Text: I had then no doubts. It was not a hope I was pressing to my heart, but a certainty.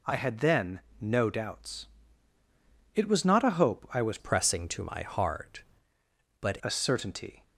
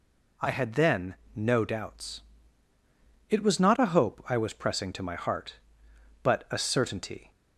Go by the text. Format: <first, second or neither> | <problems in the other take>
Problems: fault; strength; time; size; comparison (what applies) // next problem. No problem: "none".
second | pauses between "then" and "no"; slight; at 0.8 s; 0.20 s long; slight in the second // changes voice from "pressing" to "but"; from 4.1 to 6.5 s; 2.4 s long